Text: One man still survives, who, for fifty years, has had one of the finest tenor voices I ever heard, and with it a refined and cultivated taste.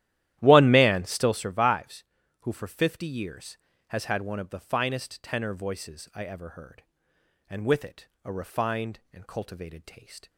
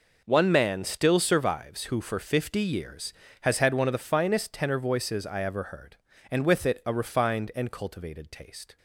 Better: second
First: starts louder than the rest; strong; until 1.5 s; 13 dB // pauses between "it" and "a"; slight; at 8.0 s; 0.16 s long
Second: none

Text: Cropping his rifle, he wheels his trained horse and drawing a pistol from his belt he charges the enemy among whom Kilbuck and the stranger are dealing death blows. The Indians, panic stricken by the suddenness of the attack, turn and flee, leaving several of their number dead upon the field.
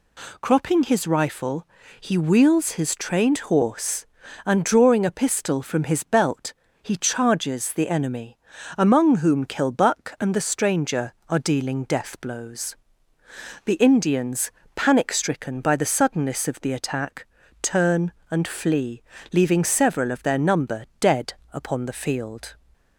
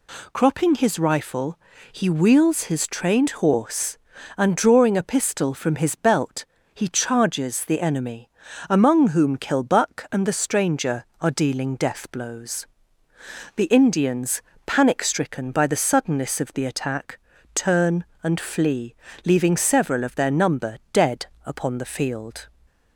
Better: neither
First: pauses between "belt" and "he"; slight; at 6.5 s; 0.30 s long // pauses between "enemy" and "among"; at 8.3 s; 0.40 s long // pauses between "number" and "dead"; slight; at 20.8 s; 0.16 s long // pauses between "dead" and "upon"; slight; at 21.3 s; 0.18 s long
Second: pauses between "belt" and "he"; slight; at 6.4 s; 0.30 s long // pauses between "enemy" and "among"; at 8.2 s; 0.40 s long // pauses between "number" and "dead"; slight; at 20.7 s; 0.16 s long // pauses between "dead" and "upon"; slight; at 21.2 s; 0.18 s long

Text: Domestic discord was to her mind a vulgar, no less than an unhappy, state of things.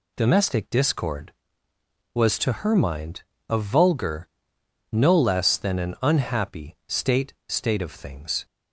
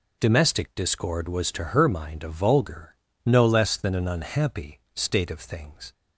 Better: second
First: pauses between "mind" and "a"; slight; at 3.2 s; 0.26 s long // says "state" twice; at 7.4 s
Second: none

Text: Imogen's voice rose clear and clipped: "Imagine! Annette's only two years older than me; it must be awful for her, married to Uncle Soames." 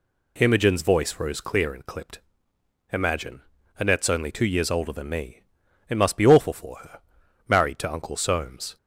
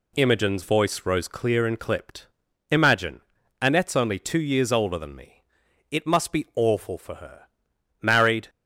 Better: first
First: none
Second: stops before "to Uncle Soames"; at 8.4 s

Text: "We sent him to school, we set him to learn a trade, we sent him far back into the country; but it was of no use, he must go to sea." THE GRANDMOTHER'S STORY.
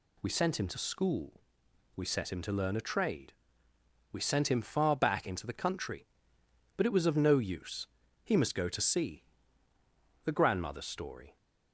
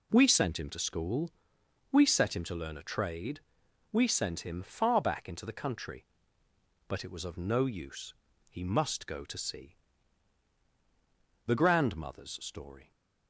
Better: neither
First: none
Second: none

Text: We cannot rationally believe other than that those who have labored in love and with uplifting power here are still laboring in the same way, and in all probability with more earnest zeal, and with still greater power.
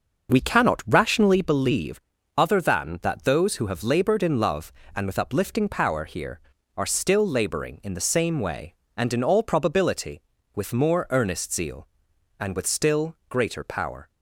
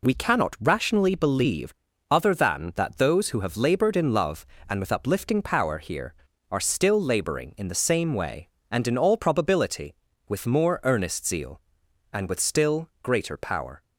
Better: second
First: starts louder than the rest; noticeable; until 1.5 s; 6 dB // pauses between "believe" and "other"; at 1.9 s; 0.38 s long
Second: pauses between "believe" and "other"; at 1.7 s; 0.38 s long

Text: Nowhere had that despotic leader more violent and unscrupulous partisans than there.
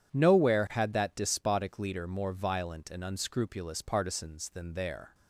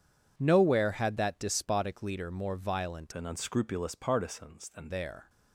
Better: first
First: none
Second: changes voice from "and" to "than"; from 3.1 to 4.8 s; 1.7 s long

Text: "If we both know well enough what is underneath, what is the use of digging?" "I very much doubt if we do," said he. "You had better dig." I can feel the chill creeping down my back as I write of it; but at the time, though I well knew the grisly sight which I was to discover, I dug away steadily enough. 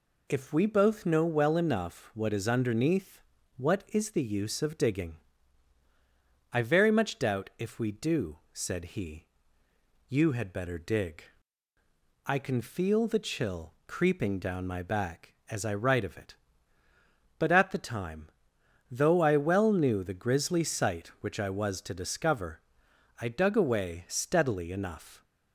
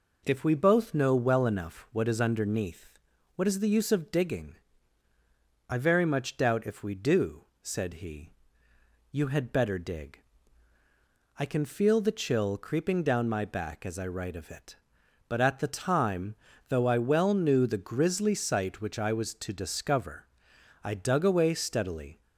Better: first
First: none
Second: stops before "enough"; at 22.2 s

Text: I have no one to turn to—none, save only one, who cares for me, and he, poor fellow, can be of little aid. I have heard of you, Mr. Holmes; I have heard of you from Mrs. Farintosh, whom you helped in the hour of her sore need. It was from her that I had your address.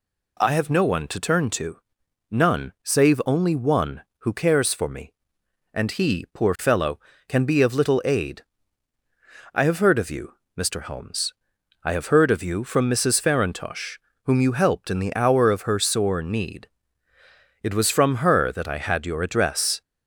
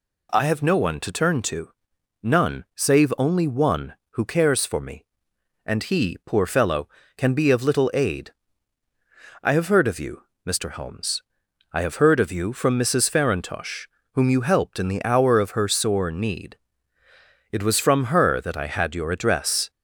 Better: neither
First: none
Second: none

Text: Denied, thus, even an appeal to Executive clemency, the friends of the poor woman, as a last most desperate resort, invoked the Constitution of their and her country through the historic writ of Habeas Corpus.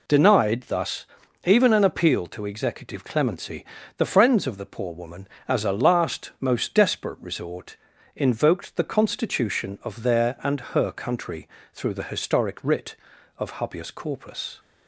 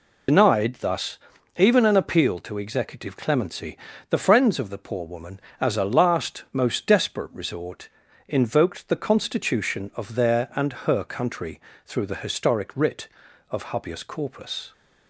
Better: first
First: pauses between "country" and "through"; slight; at 11.4 s; 0.26 s long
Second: loses the start of "Denied"; at 0.2 s; 85 ms // pauses between "country" and "through"; slight; at 11.5 s; 0.26 s long

